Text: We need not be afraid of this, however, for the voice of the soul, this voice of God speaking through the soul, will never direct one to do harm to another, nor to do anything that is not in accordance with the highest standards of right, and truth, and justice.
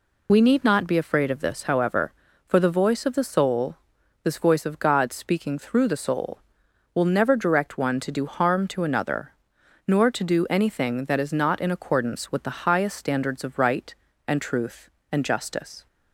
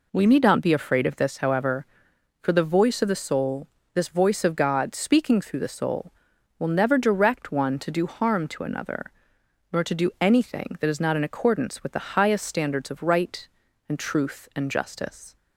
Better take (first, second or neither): second